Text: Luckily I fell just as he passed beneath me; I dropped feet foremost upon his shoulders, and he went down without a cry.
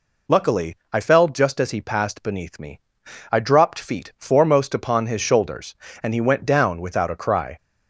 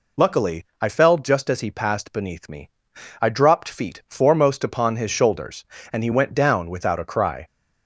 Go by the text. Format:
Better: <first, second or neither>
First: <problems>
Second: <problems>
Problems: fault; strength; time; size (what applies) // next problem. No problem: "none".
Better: neither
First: pauses between "Luckily" and "I"; slight; at 0.7 s; 0.16 s long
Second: pauses between "Luckily" and "I"; slight; at 0.6 s; 0.16 s long